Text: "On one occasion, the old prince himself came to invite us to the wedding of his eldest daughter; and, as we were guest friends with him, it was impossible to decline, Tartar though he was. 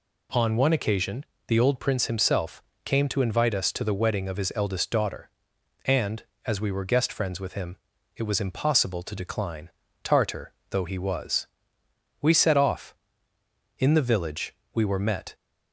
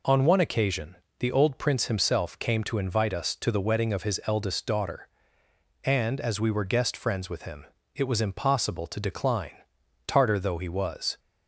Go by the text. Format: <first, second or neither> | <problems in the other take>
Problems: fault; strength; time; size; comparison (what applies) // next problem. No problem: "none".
second | pauses between "himself" and "came"; slight; at 2.6 s; 0.22 s long // pauses between "Tartar" and "though"; slight; at 10.5 s; 0.16 s long // goes on to say "We set off In the village we were met"; strong; from 12.2 s on; 3.1 s long